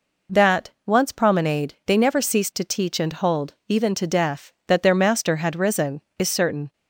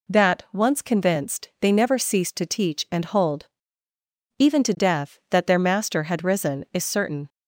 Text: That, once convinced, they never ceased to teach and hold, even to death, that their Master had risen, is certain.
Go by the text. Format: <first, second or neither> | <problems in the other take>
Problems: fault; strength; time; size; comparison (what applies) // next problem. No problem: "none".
second | says "promenade" for "convinced"; at 1.1 s